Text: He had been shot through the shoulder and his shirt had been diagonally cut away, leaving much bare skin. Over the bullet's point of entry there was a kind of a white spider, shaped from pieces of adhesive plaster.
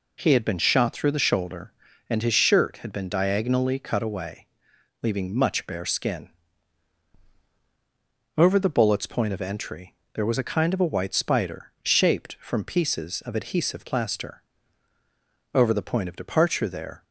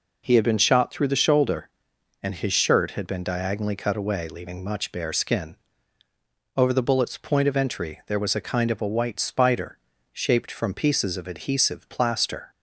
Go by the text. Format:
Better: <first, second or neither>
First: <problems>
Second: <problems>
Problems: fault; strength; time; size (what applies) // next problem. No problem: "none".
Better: second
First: pauses between "entry" and "there"; slight; at 9.9 s; 0.20 s long // goes on to say "Over the point of departure there"; from 15.5 s on; 1.5 s long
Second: none